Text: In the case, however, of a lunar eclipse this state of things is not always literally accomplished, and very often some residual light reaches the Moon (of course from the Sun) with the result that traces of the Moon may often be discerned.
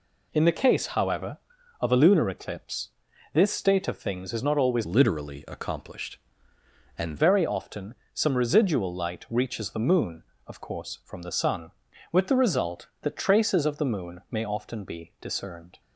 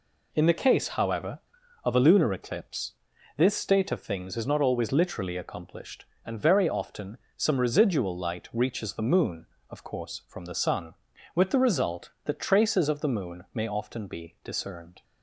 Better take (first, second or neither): second